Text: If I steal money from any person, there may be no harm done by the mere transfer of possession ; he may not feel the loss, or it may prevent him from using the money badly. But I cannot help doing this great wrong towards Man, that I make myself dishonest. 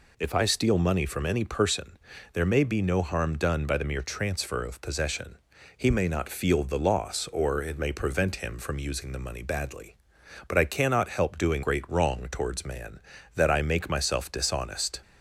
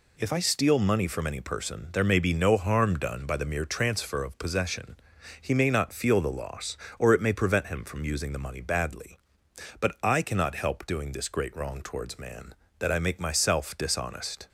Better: second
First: skips "this"; at 11.6 s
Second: none

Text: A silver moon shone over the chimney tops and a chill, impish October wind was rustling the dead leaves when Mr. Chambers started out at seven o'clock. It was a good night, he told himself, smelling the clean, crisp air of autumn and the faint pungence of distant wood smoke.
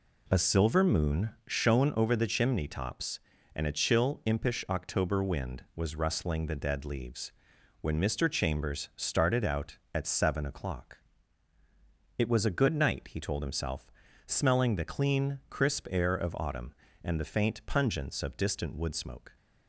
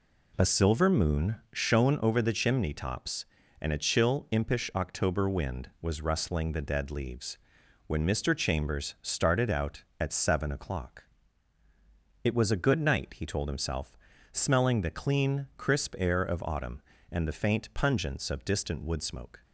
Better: neither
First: pauses between "moon" and "shone"; slight; at 1.2 s; 0.16 s long // pauses between "leaves" and "when"; noticeable; at 7.3 s; 0.48 s long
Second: pauses between "moon" and "shone"; slight; at 1.3 s; 0.16 s long // pauses between "leaves" and "when"; noticeable; at 7.3 s; 0.48 s long

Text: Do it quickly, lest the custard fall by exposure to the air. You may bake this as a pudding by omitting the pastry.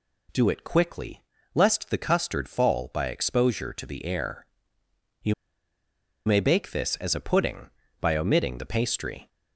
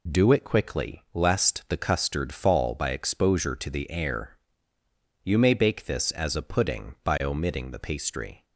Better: second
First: pauses between "You" and "may"; noticeable; at 5.3 s; 0.92 s long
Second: none

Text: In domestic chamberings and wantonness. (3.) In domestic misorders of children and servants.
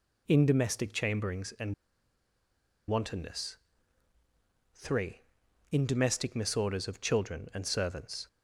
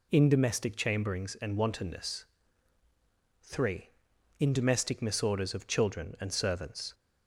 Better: second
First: pauses between "and" and "wantonness"; at 1.7 s; 1.1 s long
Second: none

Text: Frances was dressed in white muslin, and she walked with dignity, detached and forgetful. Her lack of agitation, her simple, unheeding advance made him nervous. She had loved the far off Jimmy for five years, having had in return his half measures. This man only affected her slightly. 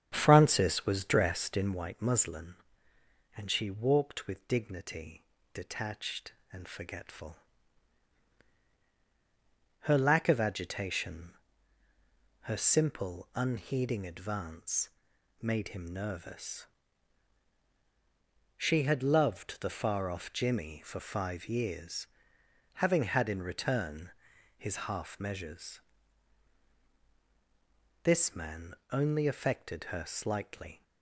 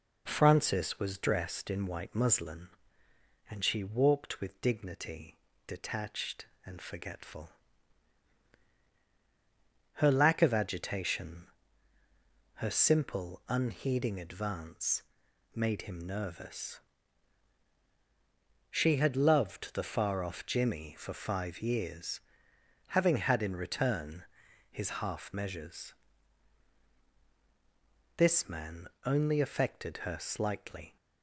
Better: second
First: starts louder than the rest; strong; until 1.8 s; 8 dB // pauses between "advance" and "made"; noticeable; at 14.8 s; 0.52 s long // pauses between "return" and "his"; noticeable; at 24.1 s; 0.46 s long // pauses between "man" and "only"; slight; at 28.7 s; 0.18 s long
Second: pauses between "advance" and "made"; noticeable; at 15.0 s; 0.52 s long // pauses between "return" and "his"; noticeable; at 24.2 s; 0.46 s long // pauses between "man" and "only"; slight; at 28.8 s; 0.18 s long

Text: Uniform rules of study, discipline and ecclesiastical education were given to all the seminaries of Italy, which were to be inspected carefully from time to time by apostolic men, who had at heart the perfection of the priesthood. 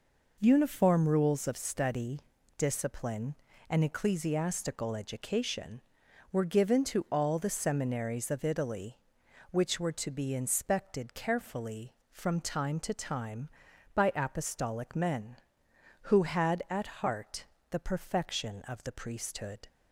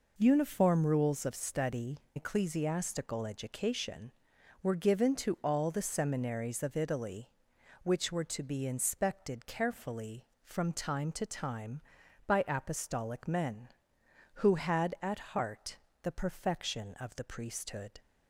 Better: first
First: pauses between "heart" and "the"; slight; at 17.4 s; 0.26 s long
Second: skips "discipline and"; at 2.0 s // pauses between "heart" and "the"; slight; at 15.7 s; 0.26 s long

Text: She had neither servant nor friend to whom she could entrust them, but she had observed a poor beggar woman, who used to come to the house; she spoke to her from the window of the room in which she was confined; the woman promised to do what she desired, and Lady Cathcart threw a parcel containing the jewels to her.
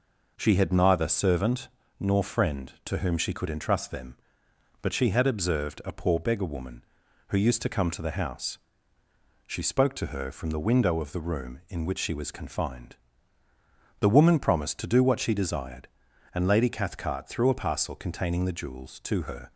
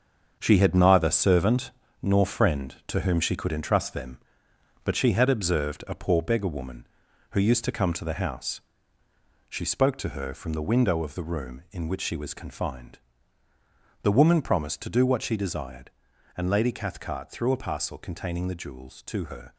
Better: first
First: pauses between "servant" and "nor"; slight; at 1.6 s; 0.28 s long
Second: gets quieter; strong; throughout; 8.5 dB // pauses between "servant" and "nor"; slight; at 1.7 s; 0.28 s long

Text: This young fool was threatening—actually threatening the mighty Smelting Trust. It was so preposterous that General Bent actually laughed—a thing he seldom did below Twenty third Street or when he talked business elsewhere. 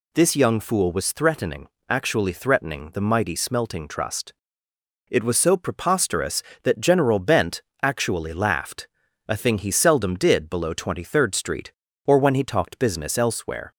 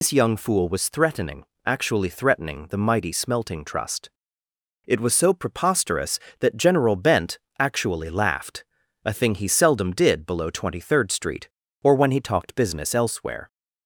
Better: first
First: pauses between "Bent" and "actually"; slight; at 7.6 s; 0.20 s long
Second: loses the start of "This"; at 0.0 s; 110 ms // pauses between "Bent" and "actually"; slight; at 7.3 s; 0.20 s long

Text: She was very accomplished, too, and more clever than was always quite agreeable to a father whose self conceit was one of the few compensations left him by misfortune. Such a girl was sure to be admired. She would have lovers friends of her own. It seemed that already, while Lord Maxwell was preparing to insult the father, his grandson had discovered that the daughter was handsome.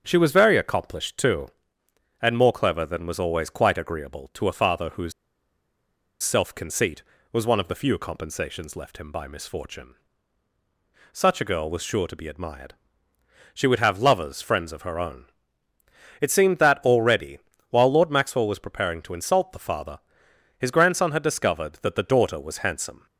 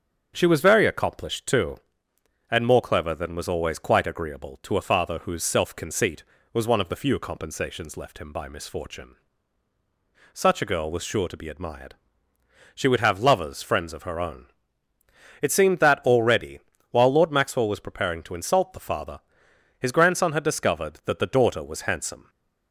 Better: second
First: starts louder than the rest; until 1.0 s; 7 dB // pauses between "whose" and "self"; at 5.1 s; 1.1 s long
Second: starts louder than the rest; until 1.3 s; 7 dB

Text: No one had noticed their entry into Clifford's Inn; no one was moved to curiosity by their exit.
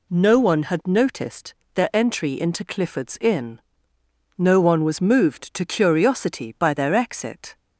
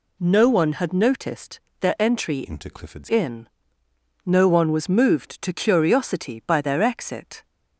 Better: first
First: pauses between "noticed" and "their"; slight; at 1.5 s; 0.20 s long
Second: pauses between "noticed" and "their"; slight; at 1.5 s; 0.20 s long // changes voice from "into" to "Clifford's"; from 2.4 to 3.0 s; 0.6 s long

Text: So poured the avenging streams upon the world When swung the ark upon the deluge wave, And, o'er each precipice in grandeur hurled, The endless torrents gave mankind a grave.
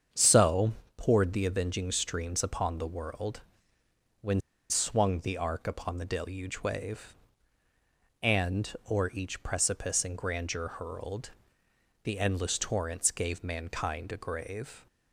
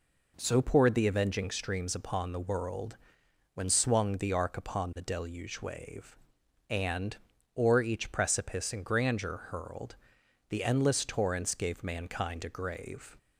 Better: second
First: starts louder than the rest; strong; until 1.3 s; 7.5 dB // pauses between "So" and "poured"; slight; at 0.7 s; 0.24 s long // pauses between "world" and "When"; noticeable; at 3.4 s; 0.78 s long // pauses between "When" and "swung"; slight; at 4.4 s; 0.29 s long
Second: pauses between "world" and "When"; noticeable; at 2.9 s; 0.56 s long

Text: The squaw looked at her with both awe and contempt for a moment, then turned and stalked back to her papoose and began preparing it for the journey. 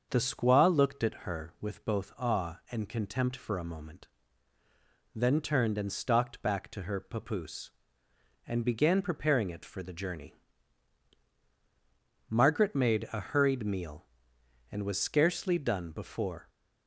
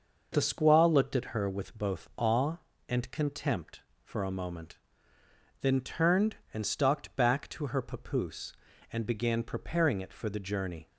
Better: second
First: starts louder than the rest; until 1.1 s; 6.5 dB // goes on to say "Margaret made a hurried meal and was scarcely done before"; strong; from 12.2 s on; 4.2 s long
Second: none

